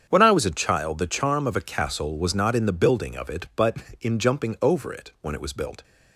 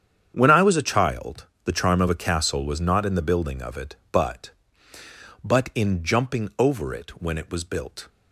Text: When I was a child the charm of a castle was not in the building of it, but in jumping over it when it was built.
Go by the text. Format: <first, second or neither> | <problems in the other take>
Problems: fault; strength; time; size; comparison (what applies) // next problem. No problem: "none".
first | starts louder than the rest; strong; until 1.3 s; 8 dB; strong in the first // pauses between "child" and "the"; slight; at 1.4 s; 0.18 s long // says "but" twice; at 5.4 s